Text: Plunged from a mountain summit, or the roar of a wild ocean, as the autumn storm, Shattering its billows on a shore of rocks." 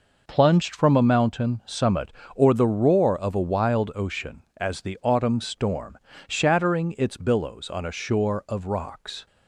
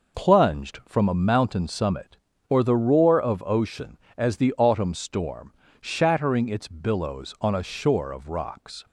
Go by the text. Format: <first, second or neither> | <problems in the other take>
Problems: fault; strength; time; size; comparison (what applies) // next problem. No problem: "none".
first | skips "a wild"; at 3.4 s